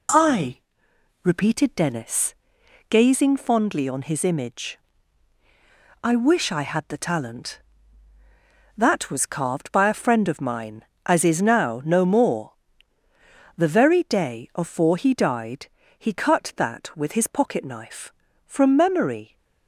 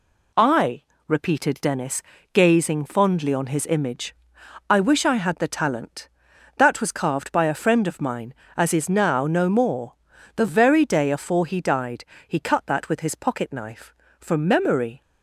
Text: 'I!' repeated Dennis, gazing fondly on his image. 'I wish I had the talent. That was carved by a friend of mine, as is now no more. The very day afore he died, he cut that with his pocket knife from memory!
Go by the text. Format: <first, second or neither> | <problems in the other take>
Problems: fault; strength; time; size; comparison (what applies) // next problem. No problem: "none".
neither | none